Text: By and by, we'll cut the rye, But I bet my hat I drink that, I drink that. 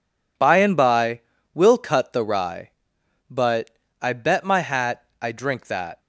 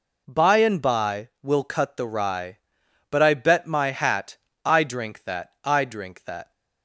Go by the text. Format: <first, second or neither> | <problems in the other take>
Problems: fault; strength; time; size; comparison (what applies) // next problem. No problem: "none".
second | pauses between "But" and "I"; slight; at 3.6 s; 0.32 s long // pauses between "hat" and "I"; slight; at 5.0 s; 0.20 s long; slight in the second // stops before "I drink that"; at 5.9 s